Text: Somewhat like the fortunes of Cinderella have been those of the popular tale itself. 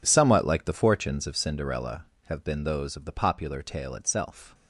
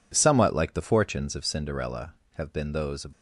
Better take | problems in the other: first | stops before "the popular tale itself"; at 3.1 s

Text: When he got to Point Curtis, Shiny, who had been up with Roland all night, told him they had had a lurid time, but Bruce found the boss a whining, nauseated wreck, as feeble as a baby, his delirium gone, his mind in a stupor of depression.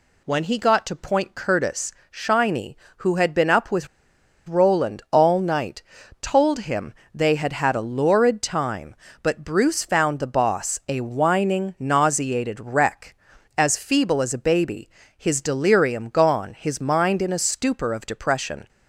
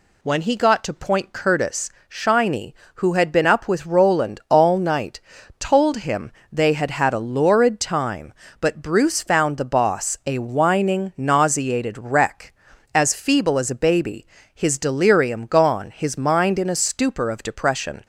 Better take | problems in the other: second | pauses between "with" and "Roland"; noticeable; at 3.8 s; 0.60 s long // pauses between "him" and "they"; slight; at 6.9 s; 0.20 s long; slight in the second

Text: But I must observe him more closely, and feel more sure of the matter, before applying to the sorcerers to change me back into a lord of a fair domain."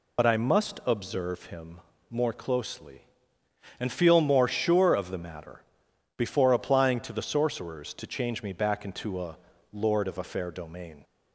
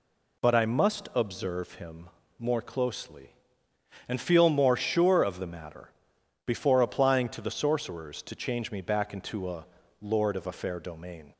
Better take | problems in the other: second | loses the start of "But"; at 0.1 s; 70 ms // pauses between "him" and "more"; slight; at 1.7 s; 0.30 s long; slight in the second // pauses between "a" and "lord"; slight; at 9.3 s; 0.36 s long; slight in the second

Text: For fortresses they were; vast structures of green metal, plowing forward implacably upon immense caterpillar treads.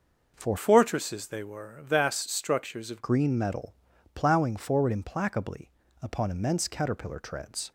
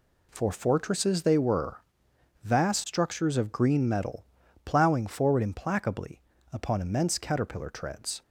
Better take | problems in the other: second | changes voice from "fortresses" to "of"; from 0.5 to 3.0 s; 2.5 s long // pauses between "implacably" and "upon"; slight; at 5.7 s; 0.30 s long; slight in the second

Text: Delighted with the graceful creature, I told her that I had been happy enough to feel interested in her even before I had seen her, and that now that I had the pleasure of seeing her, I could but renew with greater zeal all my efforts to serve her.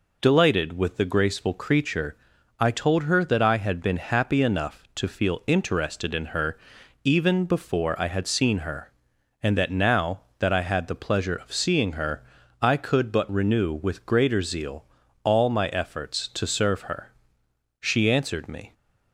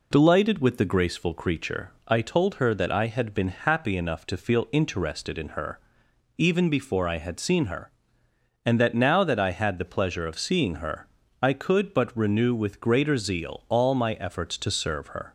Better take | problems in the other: second | pauses between "her" and "even"; noticeable; at 6.5 s; 0.48 s long; noticeable in the second // pauses between "zeal" and "all"; at 14.8 s; 0.40 s long // goes on to say "She answered me"; noticeable; from 17.8 s on; 0.92 s long

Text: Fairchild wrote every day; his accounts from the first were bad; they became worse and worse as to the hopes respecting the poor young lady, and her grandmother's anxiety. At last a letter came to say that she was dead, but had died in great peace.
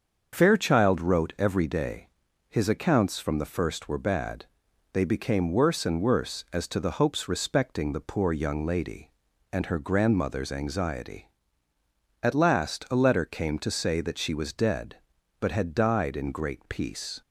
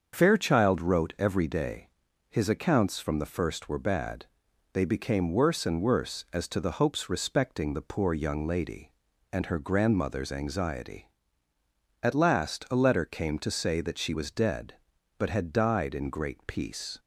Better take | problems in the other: neither | starts louder than the rest; the same in both

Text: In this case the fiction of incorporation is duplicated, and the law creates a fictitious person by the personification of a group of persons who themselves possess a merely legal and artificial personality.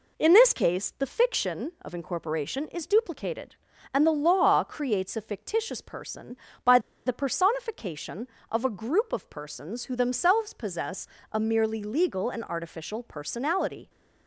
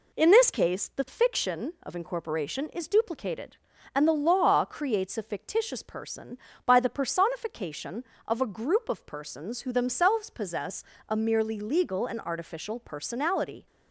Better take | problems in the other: second | pauses between "by" and "the"; slight; at 6.7 s; 0.27 s long // pauses between "possess" and "a"; slight; at 11.0 s; 0.26 s long; slight in the second

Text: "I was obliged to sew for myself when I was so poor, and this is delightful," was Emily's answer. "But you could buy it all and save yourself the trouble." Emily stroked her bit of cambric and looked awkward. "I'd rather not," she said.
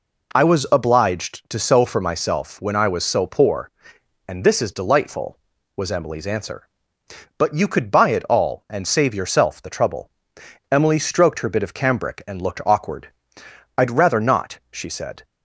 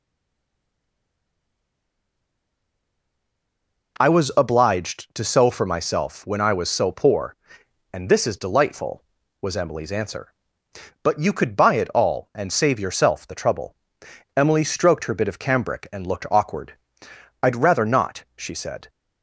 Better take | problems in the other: first | stays silent before the first word; strong; until 3.9 s; 3.9 s long

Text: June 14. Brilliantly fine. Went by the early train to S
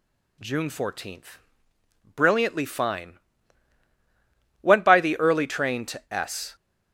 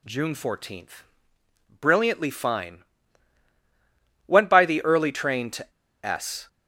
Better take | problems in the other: first | pauses between "to" and "S"; slight; at 5.7 s; 0.32 s long

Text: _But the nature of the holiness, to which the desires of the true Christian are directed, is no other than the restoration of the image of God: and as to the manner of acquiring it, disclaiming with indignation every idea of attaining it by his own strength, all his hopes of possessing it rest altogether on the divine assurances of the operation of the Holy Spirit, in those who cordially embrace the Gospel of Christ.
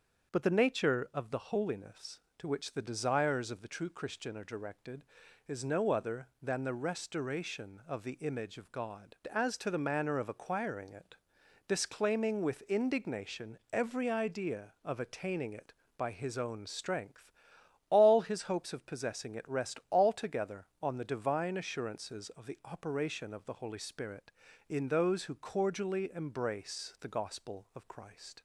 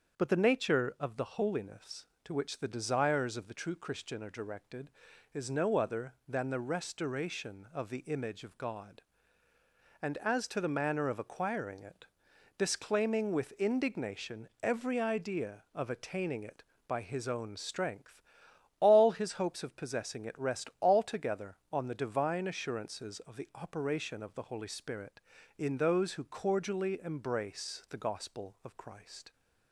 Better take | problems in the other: second | starts louder than the rest; until 1.3 s; 7 dB; also in the second // skips "and"; at 9.2 s // pauses between "indignation" and "every"; slight; at 13.5 s; 0.16 s long; slight in the second

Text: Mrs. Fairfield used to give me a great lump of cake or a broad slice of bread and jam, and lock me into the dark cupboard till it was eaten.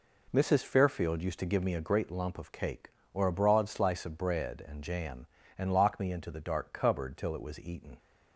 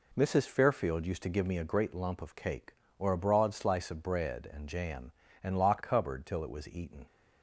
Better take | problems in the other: first | skips "me into the dark"; at 5.8 s

